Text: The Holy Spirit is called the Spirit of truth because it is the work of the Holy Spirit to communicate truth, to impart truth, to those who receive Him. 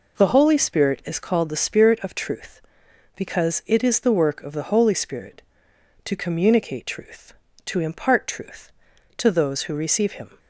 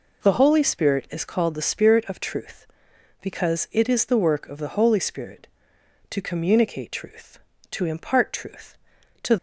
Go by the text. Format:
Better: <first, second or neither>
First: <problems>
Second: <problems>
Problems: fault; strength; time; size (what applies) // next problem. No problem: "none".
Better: first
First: none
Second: stops before "those who receive Him"; at 9.3 s